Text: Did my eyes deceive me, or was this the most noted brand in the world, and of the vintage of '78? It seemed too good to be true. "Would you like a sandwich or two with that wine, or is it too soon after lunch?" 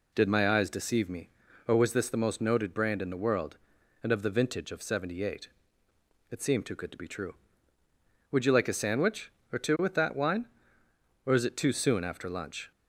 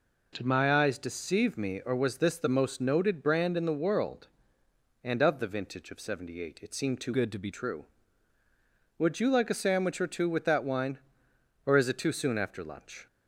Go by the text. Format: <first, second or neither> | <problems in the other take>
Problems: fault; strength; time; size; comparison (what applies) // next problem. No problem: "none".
first | changes voice from "good" to "be"; from 7.1 to 7.5 s; 0.4 s long